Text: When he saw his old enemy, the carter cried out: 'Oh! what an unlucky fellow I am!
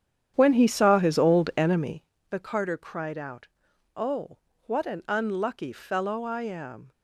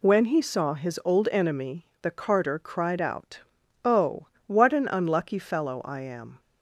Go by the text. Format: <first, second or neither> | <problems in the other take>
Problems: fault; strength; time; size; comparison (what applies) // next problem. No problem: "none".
second | starts louder than the rest; strong; until 2.0 s; 9.5 dB